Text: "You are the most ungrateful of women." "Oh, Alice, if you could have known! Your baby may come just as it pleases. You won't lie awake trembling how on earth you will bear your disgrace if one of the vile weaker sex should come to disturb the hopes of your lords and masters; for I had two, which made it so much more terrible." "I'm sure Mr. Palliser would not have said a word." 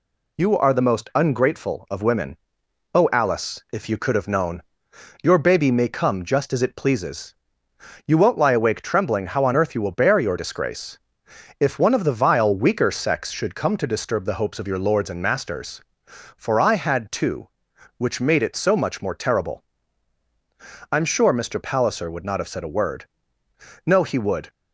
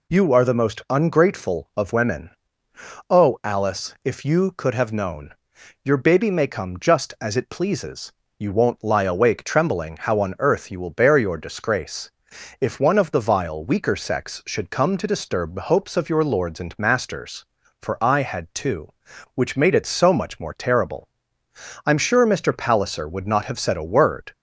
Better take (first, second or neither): second